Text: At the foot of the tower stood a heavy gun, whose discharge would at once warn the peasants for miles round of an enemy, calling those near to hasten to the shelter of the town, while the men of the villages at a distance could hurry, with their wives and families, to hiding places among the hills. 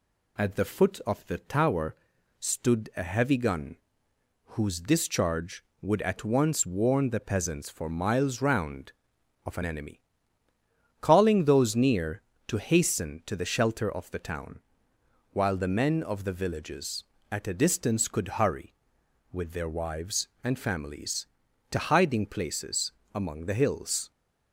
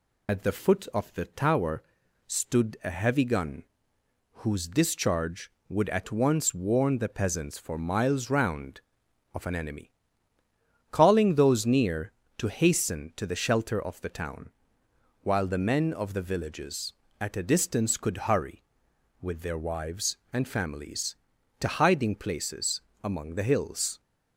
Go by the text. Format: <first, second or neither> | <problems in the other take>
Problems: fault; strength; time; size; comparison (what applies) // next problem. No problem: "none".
first | loses the start of "At"; at 0.2 s; 40 ms // pauses between "tower" and "stood"; noticeable; at 1.8 s; 0.46 s long; noticeable in the first // pauses between "places" and "among"; slight; at 22.8 s; 0.20 s long; slight in the first